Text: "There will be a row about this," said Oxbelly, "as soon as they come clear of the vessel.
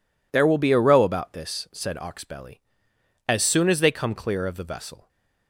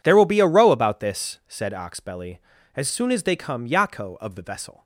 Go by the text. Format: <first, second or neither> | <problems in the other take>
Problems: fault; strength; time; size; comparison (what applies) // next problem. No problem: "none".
first | says "yako" for "clear"; at 3.6 s